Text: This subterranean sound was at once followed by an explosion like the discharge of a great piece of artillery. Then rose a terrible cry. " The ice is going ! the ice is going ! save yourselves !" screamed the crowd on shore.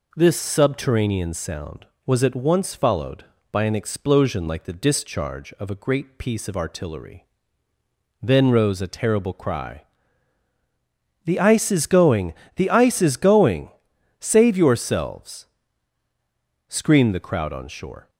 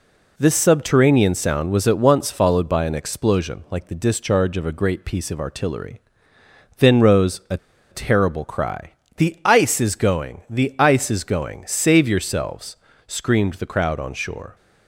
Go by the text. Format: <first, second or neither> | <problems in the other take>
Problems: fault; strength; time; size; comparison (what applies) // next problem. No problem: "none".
first | pauses between "a" and "terrible"; slight; at 7.5 s; 0.34 s long